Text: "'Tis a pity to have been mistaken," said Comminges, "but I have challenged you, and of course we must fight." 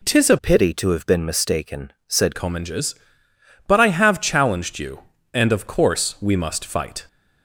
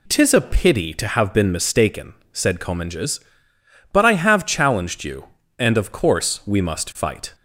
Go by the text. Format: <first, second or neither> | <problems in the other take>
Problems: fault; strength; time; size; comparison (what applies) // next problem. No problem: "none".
second | changes voice from "pity" to "said"; from 0.3 to 2.3 s; 2.0 s long